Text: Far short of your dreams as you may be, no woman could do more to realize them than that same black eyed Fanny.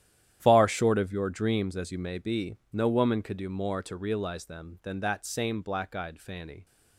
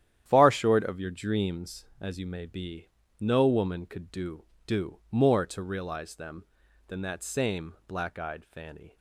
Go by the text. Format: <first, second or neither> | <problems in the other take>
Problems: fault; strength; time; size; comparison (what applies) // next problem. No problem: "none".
first | starts louder than the rest; strong; until 1.2 s; 10.5 dB; strong in the first // says "do" twice; at 4.6 s